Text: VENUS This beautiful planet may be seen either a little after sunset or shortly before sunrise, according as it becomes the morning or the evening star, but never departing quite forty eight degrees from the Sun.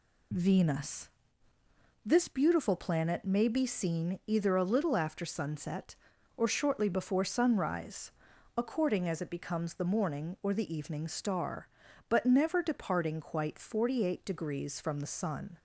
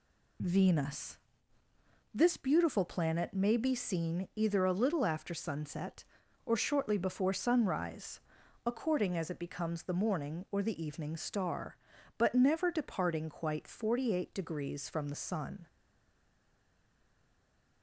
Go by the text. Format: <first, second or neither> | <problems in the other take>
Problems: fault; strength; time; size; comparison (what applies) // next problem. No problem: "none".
first | pauses between "VENUS" and "This"; noticeable; at 1.1 s; 0.96 s long; noticeable in the first // stays silent after the last word; from 15.6 s on; 2.2 s long